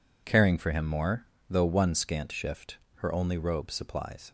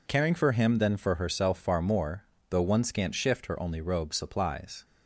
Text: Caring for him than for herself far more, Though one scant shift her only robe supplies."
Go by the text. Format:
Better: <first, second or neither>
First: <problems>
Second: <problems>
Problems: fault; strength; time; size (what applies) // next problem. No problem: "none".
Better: second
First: skips "than for herself far"; at 0.8 s // pauses between "shift" and "her"; slight; at 2.7 s; 0.18 s long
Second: none